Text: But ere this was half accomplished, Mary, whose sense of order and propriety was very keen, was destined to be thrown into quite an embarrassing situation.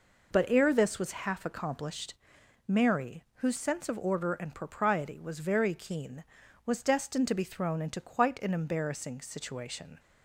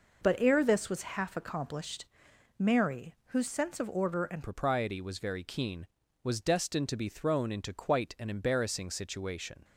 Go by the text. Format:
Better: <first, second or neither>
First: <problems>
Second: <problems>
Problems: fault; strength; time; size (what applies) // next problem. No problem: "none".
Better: first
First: none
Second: changes voice at "propriety"; from 4.4 s on; 5.2 s long